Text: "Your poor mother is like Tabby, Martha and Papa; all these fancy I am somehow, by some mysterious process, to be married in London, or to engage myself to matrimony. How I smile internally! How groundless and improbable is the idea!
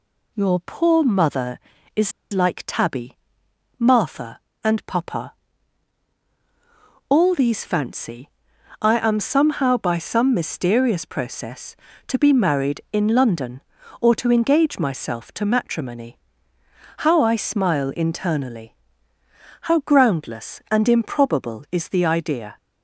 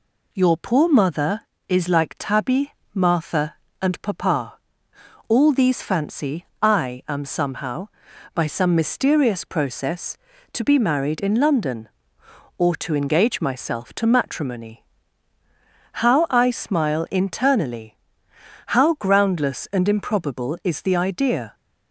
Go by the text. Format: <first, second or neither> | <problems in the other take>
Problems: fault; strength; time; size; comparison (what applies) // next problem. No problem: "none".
second | pauses between "is" and "like"; slight; at 2.1 s; 0.21 s long // pauses between "fancy" and "I"; noticeable; at 8.2 s; 0.52 s long; slight in the second